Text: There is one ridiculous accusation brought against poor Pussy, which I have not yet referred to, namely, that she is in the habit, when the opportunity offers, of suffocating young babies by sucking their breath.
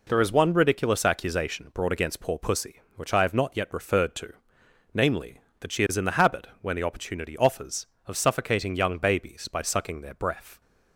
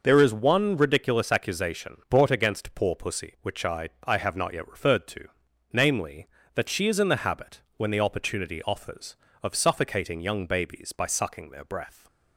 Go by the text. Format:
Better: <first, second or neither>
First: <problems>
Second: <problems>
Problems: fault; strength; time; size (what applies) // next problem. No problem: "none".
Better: first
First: none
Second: says "I" twice; at 4.0 s